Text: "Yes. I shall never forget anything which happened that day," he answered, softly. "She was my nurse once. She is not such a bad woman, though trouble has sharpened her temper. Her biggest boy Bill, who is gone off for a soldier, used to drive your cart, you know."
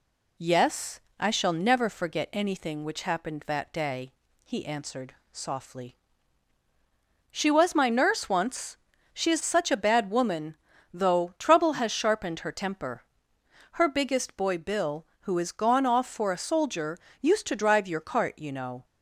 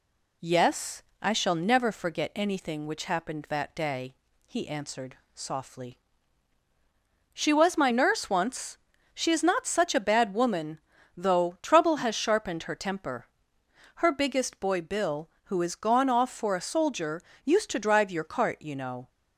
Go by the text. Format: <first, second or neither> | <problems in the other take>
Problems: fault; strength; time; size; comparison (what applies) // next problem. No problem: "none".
second | skips "not"; at 9.4 s